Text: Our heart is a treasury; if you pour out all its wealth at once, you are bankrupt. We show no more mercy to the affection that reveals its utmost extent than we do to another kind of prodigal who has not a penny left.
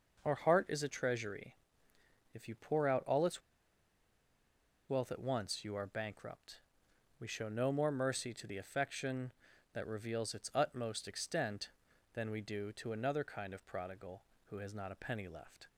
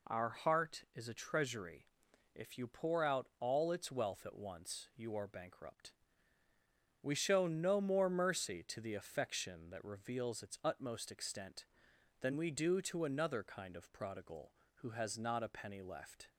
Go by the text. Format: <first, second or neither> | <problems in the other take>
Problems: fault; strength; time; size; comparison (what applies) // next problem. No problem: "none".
second | pauses between "its" and "wealth"; strong; at 3.4 s; 1.4 s long